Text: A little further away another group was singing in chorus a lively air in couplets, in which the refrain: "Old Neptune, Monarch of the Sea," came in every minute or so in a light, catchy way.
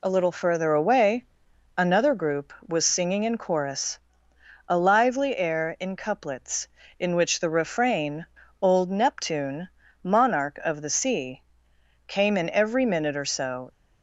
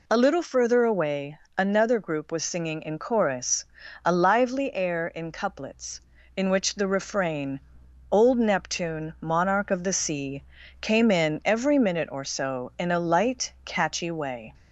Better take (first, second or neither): second